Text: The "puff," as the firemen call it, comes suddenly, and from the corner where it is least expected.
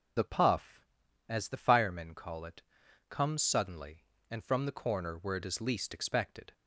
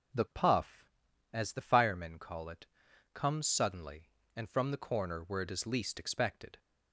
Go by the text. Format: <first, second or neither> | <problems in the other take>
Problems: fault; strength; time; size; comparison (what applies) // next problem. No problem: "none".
second | loses the start of "The"; at 0.1 s; 40 ms